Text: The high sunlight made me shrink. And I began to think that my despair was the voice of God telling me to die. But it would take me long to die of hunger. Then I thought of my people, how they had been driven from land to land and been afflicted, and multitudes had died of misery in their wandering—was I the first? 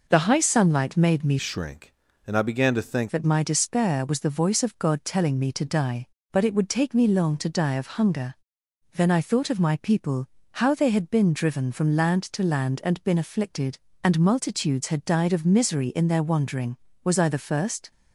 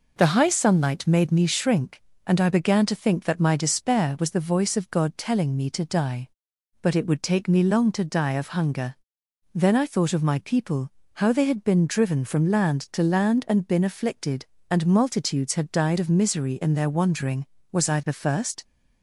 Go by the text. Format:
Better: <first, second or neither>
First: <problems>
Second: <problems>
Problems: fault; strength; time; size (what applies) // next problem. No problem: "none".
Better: second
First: changes voice from "shrink" to "think"; from 1.3 to 3.1 s; 1.8 s long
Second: none